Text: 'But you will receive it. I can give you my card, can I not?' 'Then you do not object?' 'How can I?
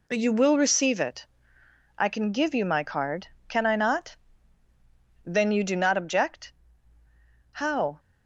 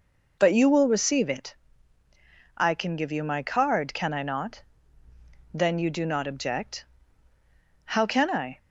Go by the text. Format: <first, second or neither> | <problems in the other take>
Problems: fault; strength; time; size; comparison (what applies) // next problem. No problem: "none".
second | stops before "can I"; at 7.9 s